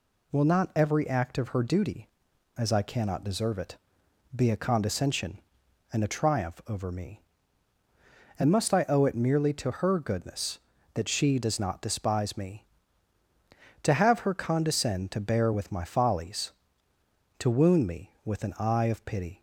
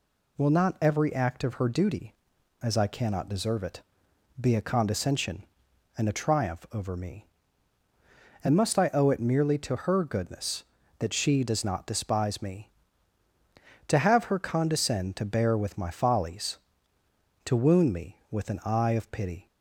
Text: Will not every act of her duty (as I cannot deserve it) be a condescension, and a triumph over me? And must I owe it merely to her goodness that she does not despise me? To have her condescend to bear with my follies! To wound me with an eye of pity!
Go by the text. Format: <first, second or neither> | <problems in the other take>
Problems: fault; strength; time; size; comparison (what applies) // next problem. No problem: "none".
neither | none